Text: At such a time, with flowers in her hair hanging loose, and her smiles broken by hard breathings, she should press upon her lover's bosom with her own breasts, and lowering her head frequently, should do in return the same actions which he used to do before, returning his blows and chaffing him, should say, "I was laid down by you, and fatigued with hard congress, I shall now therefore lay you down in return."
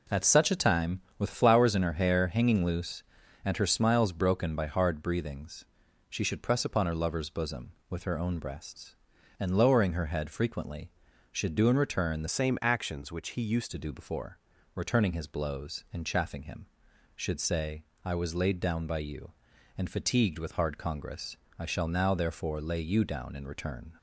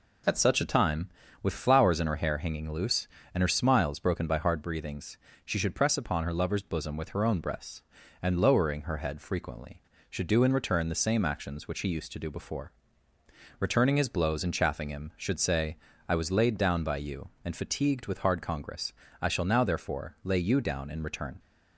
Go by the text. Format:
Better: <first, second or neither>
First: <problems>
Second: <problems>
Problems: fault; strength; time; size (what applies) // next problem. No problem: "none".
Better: second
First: changes voice from "same" to "used"; from 12.2 to 13.7 s; 1.5 s long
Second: none